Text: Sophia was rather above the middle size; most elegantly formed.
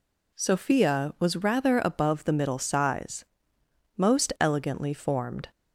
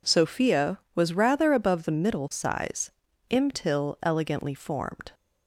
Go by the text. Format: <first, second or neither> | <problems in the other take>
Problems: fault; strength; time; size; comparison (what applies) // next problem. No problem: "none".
first | says "imtil" for "most"; at 3.2 s